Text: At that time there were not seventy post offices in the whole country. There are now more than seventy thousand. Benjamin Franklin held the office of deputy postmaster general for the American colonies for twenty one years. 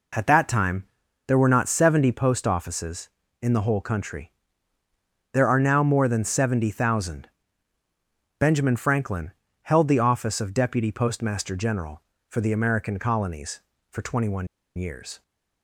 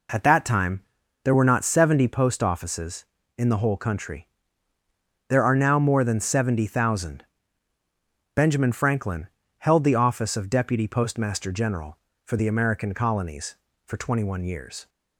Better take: second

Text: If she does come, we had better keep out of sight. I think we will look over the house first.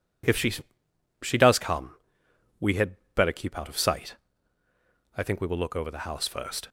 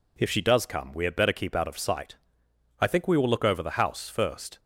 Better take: second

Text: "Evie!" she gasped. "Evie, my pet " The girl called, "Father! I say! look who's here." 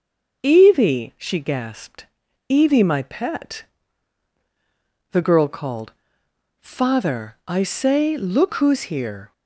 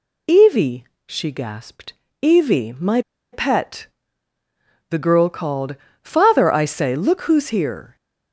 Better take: first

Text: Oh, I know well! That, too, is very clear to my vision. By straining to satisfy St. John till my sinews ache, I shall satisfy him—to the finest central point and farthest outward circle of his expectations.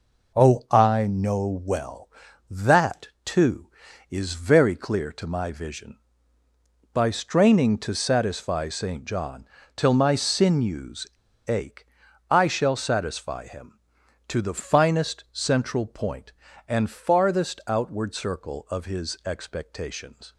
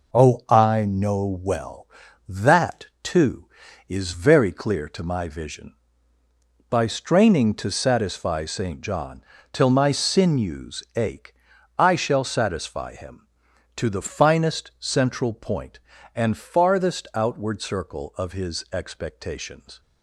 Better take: second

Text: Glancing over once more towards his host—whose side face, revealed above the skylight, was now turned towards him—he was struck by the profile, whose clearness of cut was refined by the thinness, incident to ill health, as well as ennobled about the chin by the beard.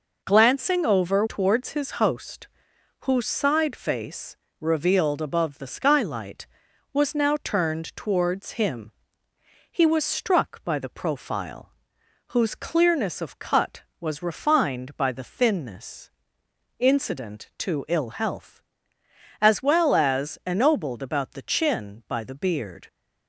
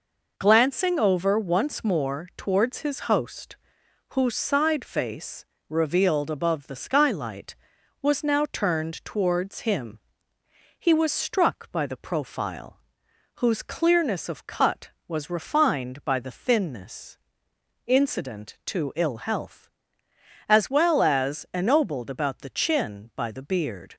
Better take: second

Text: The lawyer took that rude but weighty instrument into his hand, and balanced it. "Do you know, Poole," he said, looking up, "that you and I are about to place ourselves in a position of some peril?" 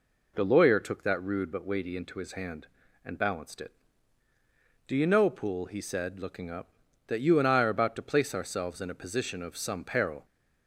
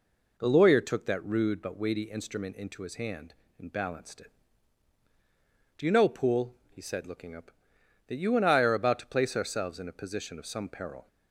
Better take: second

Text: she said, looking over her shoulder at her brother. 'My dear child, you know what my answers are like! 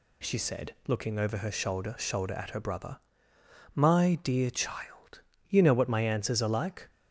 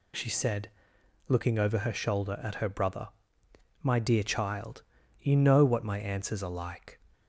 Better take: second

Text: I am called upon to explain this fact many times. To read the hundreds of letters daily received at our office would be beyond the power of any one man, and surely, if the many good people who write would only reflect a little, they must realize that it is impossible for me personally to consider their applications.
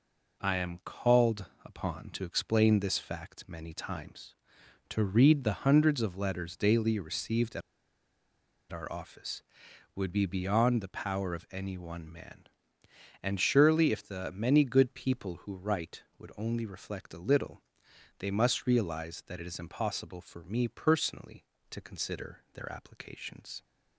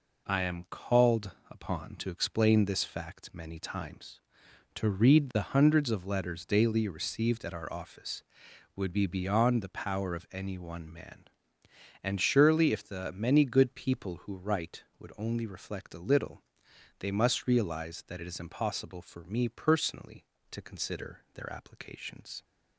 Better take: second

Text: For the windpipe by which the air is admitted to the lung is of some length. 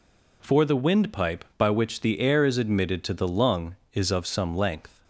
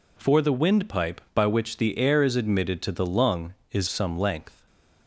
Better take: first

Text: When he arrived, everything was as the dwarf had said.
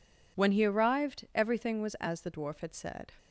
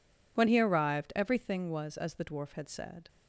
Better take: neither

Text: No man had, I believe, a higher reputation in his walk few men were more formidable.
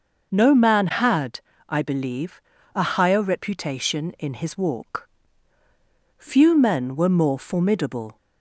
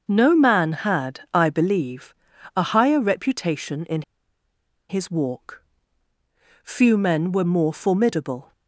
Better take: first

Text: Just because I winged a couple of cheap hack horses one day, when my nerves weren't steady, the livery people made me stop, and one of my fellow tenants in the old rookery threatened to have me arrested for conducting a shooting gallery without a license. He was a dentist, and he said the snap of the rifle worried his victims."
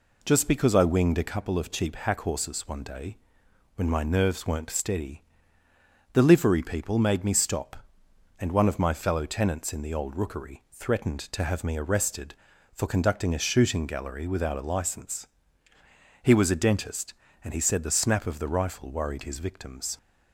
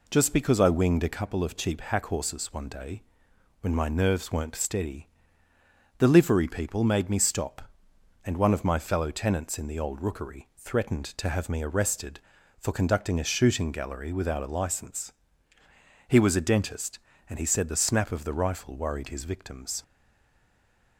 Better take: first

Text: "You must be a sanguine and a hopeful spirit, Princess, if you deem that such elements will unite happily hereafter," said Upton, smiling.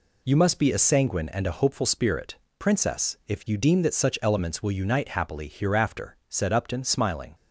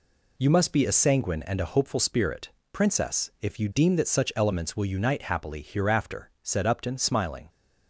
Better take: neither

